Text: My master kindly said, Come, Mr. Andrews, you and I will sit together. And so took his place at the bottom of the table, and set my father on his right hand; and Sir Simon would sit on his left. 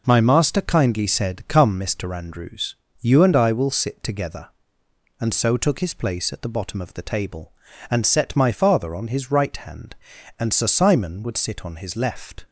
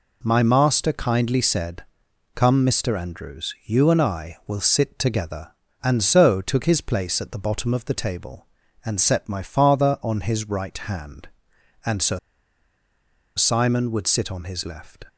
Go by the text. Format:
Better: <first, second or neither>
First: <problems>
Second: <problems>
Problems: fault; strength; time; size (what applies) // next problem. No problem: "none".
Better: first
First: none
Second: pauses between "Sir" and "Simon"; at 12.1 s; 1.1 s long